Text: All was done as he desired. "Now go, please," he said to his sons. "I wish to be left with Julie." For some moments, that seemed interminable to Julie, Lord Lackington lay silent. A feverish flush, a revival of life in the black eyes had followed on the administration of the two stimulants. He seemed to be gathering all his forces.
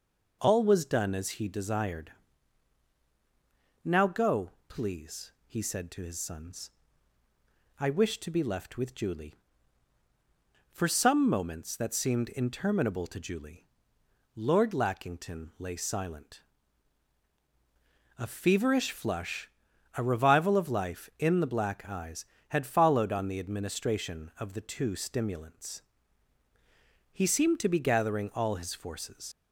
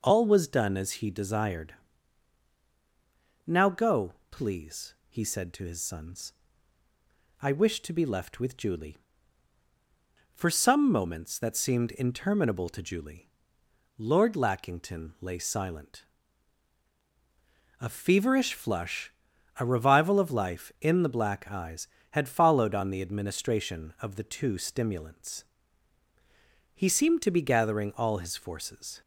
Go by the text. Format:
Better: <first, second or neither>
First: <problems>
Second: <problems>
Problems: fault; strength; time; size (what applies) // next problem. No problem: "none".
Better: second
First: leaves "forces" unfinished; at 29.3 s; 70 ms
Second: none